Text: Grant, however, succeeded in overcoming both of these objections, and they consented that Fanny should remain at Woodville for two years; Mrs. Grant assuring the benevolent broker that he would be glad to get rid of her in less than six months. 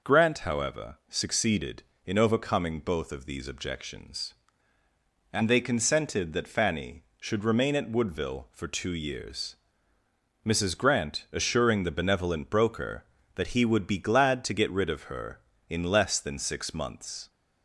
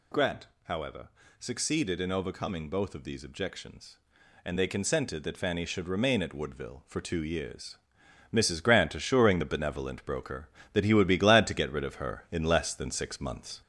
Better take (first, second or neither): first